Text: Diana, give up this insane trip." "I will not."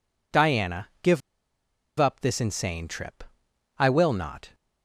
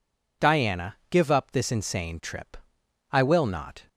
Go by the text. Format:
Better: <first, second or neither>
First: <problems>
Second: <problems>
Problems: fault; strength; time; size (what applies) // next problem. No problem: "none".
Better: second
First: pauses between "give" and "up"; noticeable; at 1.2 s; 0.79 s long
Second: none